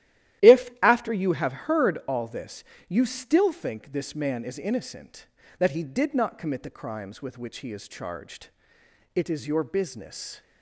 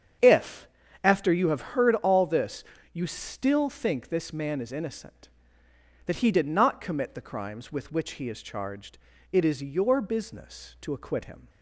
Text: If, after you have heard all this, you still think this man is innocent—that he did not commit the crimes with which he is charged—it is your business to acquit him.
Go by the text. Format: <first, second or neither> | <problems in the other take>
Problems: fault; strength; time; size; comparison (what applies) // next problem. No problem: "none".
second | starts louder than the rest; strong; until 1.5 s; 13 dB; strong in the second // stops before "to acquit him"; at 10.4 s